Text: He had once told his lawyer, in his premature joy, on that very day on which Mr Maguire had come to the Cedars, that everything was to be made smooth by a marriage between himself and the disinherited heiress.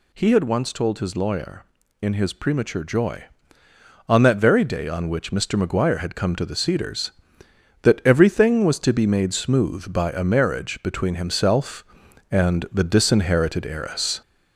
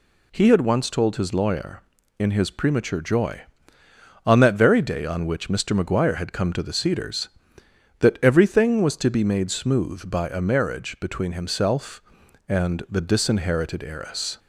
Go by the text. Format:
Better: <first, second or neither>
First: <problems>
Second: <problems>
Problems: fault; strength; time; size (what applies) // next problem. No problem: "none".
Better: second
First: gets louder; slight; throughout; 3 dB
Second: none